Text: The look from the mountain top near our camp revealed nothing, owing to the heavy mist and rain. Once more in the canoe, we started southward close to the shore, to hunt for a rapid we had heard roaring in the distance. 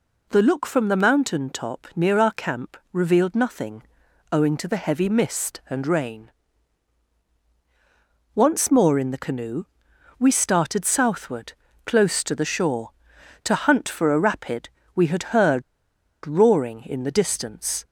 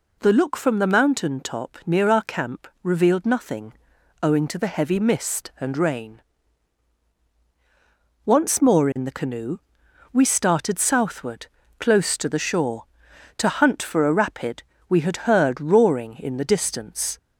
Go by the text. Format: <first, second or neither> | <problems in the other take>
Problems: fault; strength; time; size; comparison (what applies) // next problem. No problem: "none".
second | pauses between "camp" and "revealed"; slight; at 2.7 s; 0.16 s long; slight in the second // pauses between "southward" and "close"; slight; at 11.5 s; 0.32 s long; slight in the second // pauses between "rapid" and "we"; slight; at 14.6 s; 0.26 s long; slight in the second // pauses between "heard" and "roaring"; noticeable; at 15.6 s; 0.63 s long